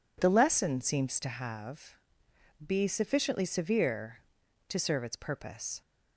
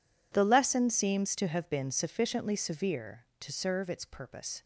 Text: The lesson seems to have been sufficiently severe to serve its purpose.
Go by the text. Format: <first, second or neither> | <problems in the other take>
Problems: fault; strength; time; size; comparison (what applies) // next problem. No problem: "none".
second | says "be" for "been"; at 2.6 s